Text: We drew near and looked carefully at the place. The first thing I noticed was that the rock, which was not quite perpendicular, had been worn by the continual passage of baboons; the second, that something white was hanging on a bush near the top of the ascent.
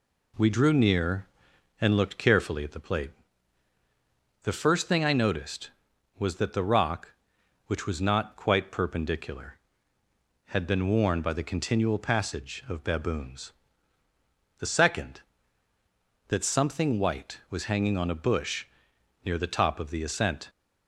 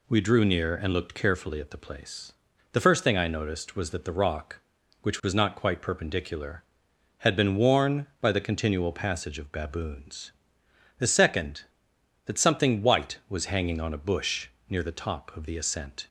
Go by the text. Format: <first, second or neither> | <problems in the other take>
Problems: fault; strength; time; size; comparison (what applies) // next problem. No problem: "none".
second | says "plate" for "place"; at 2.7 s // pauses between "bush" and "near"; noticeable; at 18.6 s; 0.58 s long; slight in the second